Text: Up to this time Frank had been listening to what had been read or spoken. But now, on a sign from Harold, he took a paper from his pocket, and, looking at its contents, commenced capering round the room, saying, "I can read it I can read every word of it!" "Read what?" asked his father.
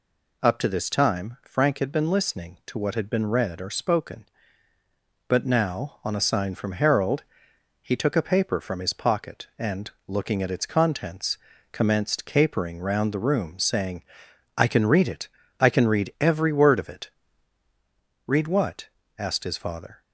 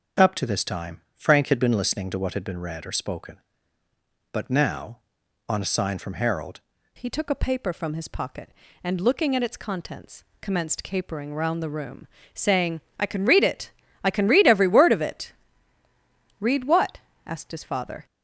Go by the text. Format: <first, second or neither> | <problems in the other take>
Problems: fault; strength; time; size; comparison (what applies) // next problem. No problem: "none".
first | starts louder than the rest; until 1.3 s; 6 dB // changes voice at "he"; from 6.9 s on; 11.1 s long // pauses between "it" and "I"; slight; at 13.7 s; 0.32 s long; slight in the first